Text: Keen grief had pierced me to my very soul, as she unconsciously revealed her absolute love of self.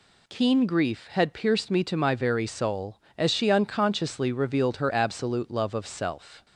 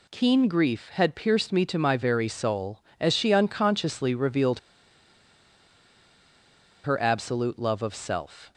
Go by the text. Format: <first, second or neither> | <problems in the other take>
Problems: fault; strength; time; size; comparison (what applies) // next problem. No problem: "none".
first | pauses between "revealed" and "her"; strong; at 4.5 s; 2.2 s long